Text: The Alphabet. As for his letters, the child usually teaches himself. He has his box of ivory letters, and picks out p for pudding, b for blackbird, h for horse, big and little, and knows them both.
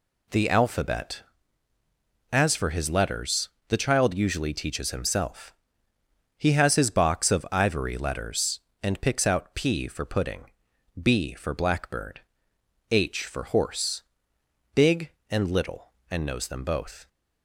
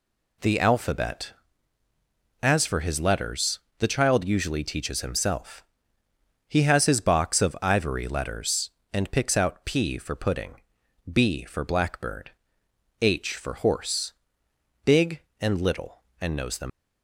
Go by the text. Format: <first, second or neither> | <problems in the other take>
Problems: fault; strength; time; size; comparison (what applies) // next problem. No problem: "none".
first | stops before "both"; at 16.6 s